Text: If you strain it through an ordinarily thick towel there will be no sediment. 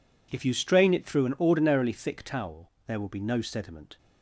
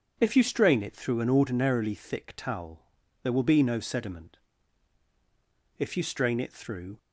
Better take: first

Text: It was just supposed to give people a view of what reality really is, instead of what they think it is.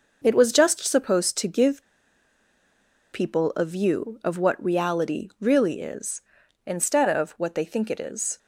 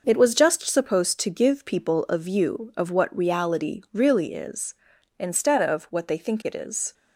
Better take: second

